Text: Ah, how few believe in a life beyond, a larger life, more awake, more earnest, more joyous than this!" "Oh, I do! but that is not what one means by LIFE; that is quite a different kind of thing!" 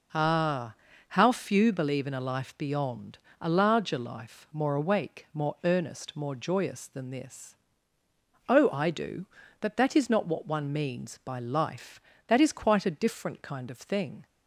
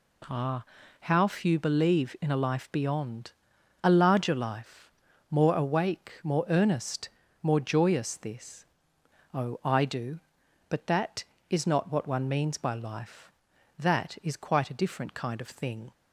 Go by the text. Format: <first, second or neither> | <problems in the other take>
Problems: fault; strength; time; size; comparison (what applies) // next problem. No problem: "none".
first | skips "than"; at 8.1 s